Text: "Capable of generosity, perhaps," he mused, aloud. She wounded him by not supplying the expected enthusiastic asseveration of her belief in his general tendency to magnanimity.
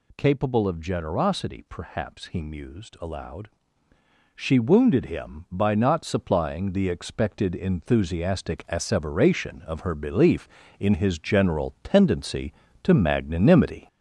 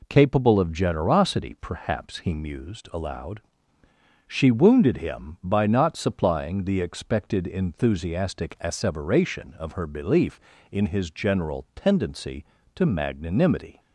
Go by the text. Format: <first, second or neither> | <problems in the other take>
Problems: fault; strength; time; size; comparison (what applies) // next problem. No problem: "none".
second | gets louder; noticeable; throughout; 5.5 dB